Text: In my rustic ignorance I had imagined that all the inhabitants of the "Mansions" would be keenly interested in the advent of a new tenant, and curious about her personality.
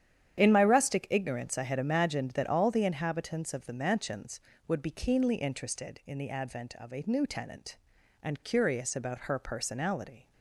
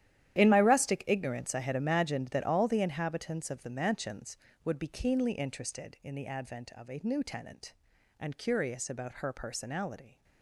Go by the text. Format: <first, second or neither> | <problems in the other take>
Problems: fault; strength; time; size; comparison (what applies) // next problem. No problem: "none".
first | gets quieter; strong; throughout; 15 dB // starts louder than the rest; strong; until 1.4 s; 11 dB; strong in the first